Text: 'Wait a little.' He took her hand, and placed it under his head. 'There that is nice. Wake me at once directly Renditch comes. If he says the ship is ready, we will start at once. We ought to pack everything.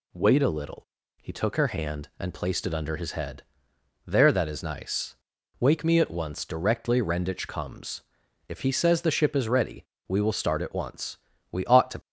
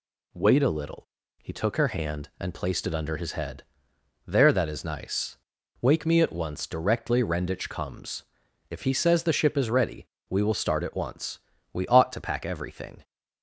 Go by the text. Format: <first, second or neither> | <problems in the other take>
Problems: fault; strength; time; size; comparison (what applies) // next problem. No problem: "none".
second | stops before "pack everything"; at 12.0 s